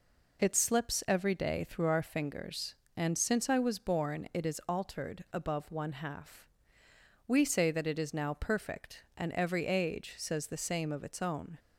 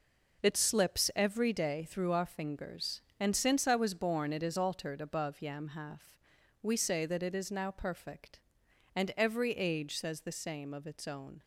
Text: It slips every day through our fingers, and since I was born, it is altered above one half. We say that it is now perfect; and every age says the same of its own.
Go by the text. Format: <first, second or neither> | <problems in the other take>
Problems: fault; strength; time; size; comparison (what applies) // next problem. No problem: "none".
first | says "yam" for "one"; at 5.4 s